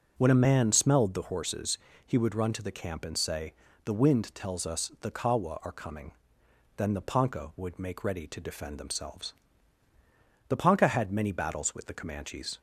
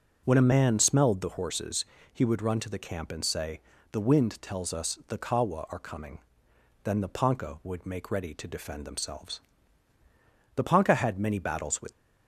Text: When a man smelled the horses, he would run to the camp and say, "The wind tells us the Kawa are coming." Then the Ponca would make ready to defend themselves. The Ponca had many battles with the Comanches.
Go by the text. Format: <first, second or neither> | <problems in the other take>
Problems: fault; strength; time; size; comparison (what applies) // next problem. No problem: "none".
first | stops before "the Comanches"; at 11.9 s